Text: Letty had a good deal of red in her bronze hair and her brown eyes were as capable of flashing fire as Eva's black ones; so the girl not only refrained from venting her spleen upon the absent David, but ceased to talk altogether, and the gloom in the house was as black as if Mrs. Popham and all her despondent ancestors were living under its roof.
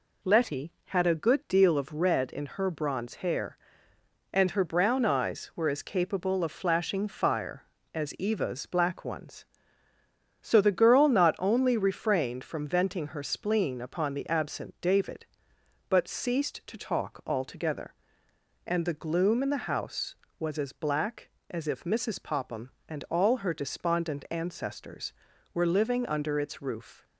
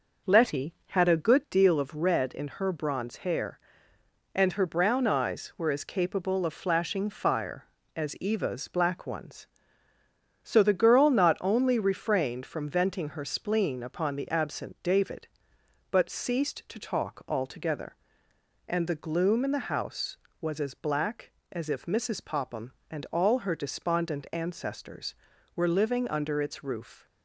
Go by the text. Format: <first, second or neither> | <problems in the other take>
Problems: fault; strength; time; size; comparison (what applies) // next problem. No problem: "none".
first | starts louder than the rest; noticeable; until 1.5 s; 5.5 dB